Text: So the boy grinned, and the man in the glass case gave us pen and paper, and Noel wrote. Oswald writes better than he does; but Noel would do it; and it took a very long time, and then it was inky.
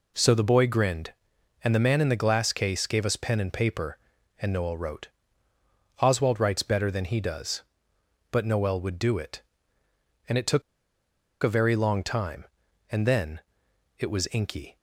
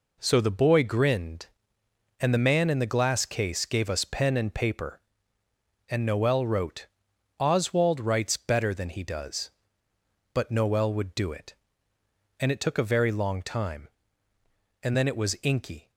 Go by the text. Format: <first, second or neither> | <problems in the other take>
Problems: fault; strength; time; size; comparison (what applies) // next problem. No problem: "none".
second | pauses between "took" and "a"; noticeable; at 10.6 s; 0.80 s long // pauses between "then" and "it"; noticeable; at 13.4 s; 0.56 s long